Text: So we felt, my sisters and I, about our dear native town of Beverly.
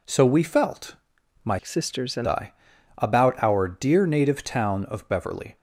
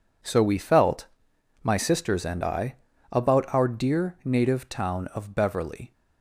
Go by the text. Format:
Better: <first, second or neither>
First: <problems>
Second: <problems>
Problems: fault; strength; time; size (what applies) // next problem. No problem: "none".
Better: second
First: changes voice from "sisters" to "and"; from 1.6 to 2.2 s; 0.6 s long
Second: none